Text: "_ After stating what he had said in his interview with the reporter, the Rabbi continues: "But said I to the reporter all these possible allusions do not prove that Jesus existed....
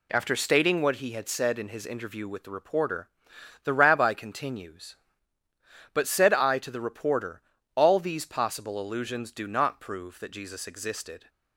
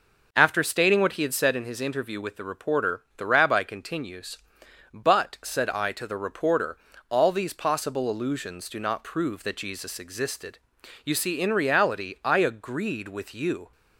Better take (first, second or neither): first